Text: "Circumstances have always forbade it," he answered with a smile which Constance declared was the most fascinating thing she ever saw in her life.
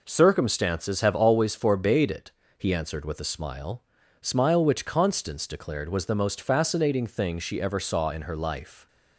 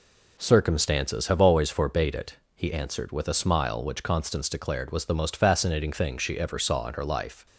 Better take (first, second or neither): second